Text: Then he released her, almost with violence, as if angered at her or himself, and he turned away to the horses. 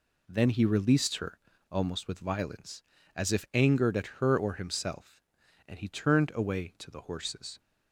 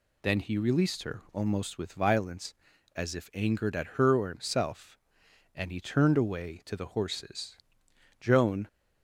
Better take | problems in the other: first | goes on to say "Joan"; slight; from 8.1 s on; 0.48 s long

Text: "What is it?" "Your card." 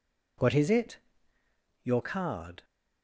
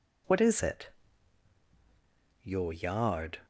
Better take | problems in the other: first | says "yard" for "card"; at 2.7 s

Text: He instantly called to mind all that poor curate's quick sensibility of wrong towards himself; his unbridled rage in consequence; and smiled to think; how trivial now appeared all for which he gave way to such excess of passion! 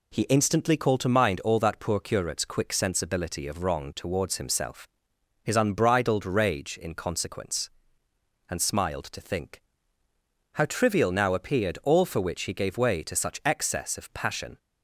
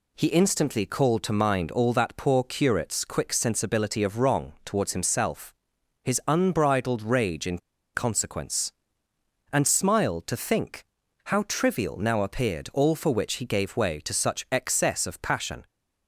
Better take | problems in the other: first | pauses between "in" and "consequence"; at 7.5 s; 0.37 s long

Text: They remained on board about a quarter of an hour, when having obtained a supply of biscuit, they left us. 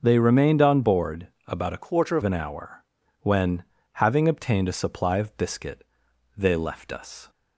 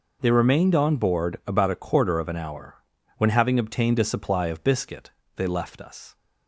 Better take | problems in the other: second | pauses between "board" and "about"; slight; at 1.2 s; 0.18 s long // changes voice from "quarter" to "of"; from 1.8 to 2.2 s; 0.4 s long // pauses between "when" and "having"; slight; at 3.6 s; 0.30 s long

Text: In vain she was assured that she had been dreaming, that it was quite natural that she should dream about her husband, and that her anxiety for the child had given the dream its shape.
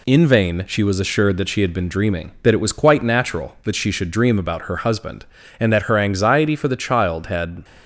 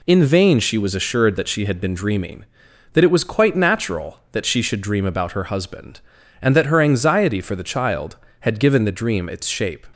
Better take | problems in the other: second | stops before "given the dream its shape"; at 7.6 s

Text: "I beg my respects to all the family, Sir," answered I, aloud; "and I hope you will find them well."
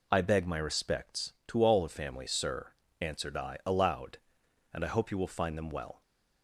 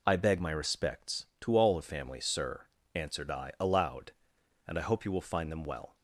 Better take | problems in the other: neither | none

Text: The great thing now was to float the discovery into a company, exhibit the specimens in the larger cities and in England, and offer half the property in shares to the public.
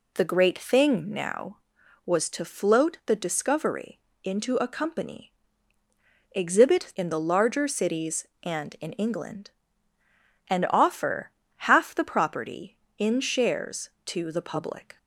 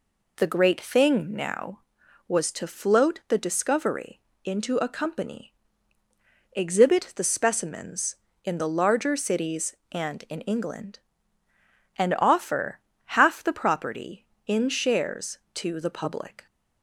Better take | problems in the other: second | pauses between "discovery" and "into"; slight; at 3.9 s; 0.24 s long; slight in the second // skips "the specimens"; at 6.9 s // pauses between "offer" and "half"; slight; at 11.3 s; 0.26 s long; slight in the second

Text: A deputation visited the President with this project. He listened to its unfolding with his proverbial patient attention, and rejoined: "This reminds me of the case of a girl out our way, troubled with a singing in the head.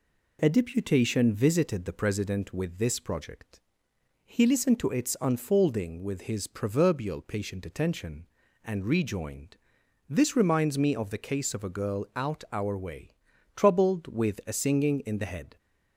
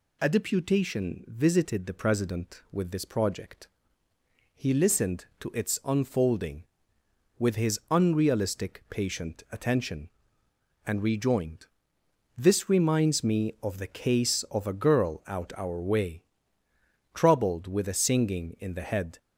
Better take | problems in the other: first | says "unrealistic" for "proverbial"; at 7.8 s

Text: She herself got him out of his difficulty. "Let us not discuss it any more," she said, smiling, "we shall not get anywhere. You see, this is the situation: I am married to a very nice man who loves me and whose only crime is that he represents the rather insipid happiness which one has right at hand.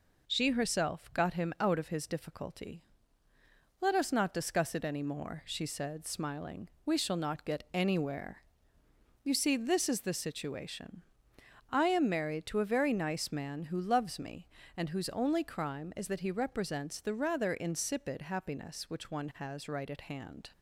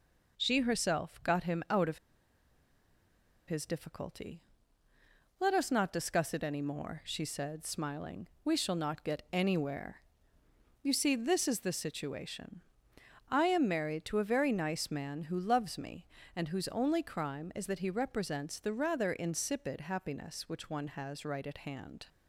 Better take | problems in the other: first | pauses between "of" and "his"; strong; at 1.9 s; 1.4 s long

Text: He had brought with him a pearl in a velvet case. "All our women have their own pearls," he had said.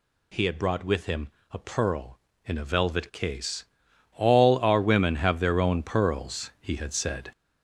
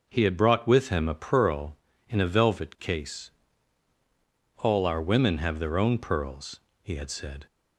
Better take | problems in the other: second | gets louder; noticeable; throughout; 5.5 dB // pauses between "him" and "a"; slight; at 1.3 s; 0.20 s long

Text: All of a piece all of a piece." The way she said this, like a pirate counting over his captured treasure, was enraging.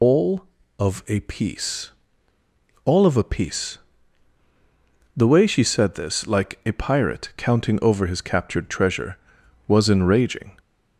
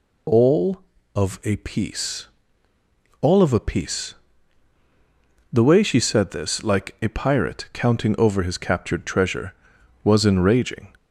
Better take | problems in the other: second | loses the start of "All"; at 0.0 s; 105 ms // pauses between "piece" and "all"; noticeable; at 1.8 s; 0.96 s long; noticeable in the second

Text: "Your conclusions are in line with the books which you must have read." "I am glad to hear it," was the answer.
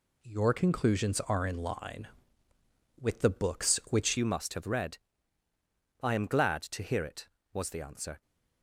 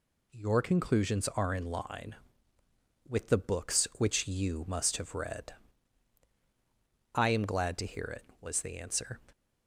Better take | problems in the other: second | changes voice at "you"; from 4.1 s on; 4.1 s long

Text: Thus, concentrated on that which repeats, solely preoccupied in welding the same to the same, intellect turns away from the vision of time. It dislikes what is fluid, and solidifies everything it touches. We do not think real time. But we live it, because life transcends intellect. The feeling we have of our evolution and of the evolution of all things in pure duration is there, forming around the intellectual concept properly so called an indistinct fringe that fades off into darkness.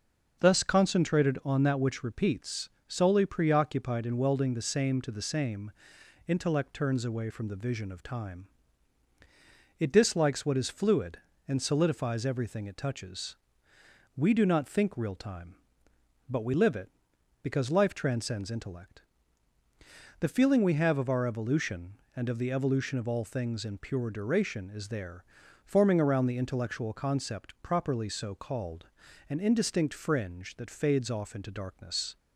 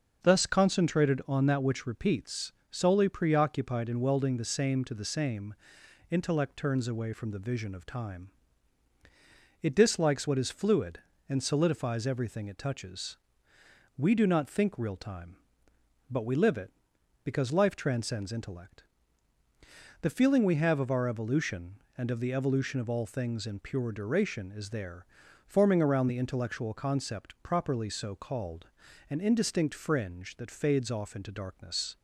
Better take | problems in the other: neither | starts louder than the rest; the same in both // pauses between "called" and "an"; the same in both

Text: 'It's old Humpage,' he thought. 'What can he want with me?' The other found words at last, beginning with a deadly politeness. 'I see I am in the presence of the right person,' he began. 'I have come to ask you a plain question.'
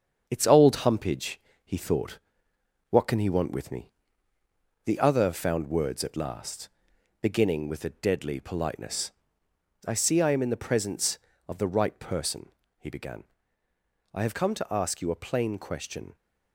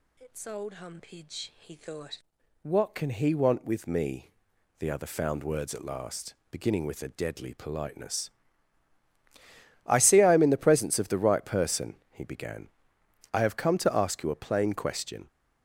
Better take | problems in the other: second | gets quieter; noticeable; throughout; 4.5 dB

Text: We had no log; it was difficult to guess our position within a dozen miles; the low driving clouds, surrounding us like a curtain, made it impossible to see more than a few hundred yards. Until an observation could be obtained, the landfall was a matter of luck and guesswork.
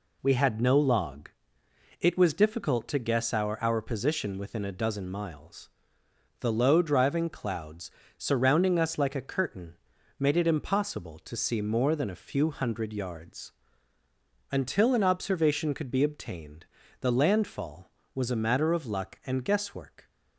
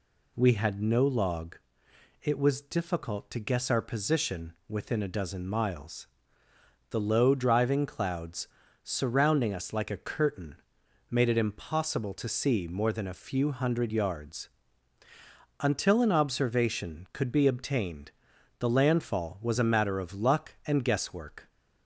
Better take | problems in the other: second | says "our" twice; at 3.6 s

